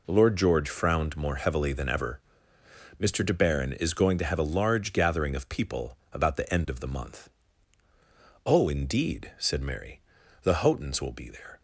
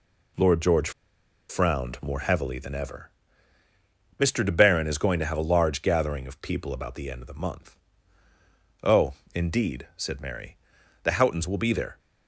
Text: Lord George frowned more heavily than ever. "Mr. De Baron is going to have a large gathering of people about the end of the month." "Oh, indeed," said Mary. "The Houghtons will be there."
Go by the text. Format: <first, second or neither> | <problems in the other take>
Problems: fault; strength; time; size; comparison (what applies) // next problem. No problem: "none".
first | pauses between "George" and "frowned"; noticeable; at 0.8 s; 0.59 s long